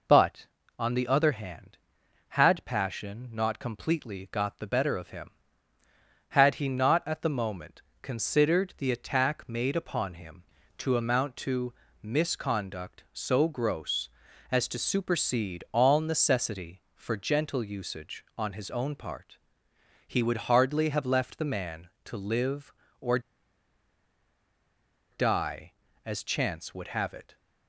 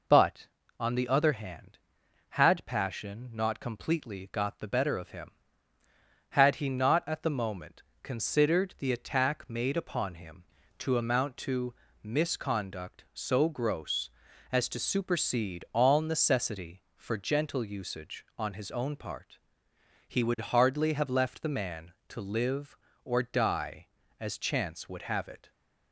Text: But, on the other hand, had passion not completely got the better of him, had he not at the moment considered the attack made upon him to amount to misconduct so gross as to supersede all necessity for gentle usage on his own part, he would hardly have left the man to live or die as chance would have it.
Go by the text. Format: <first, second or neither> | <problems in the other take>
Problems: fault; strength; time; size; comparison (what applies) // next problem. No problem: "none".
second | pauses between "moment" and "considered"; slight; at 7.8 s; 0.20 s long; slight in the second // pauses between "to" and "misconduct"; slight; at 11.7 s; 0.30 s long; slight in the second // pauses between "or" and "die"; strong; at 23.1 s; 1.9 s long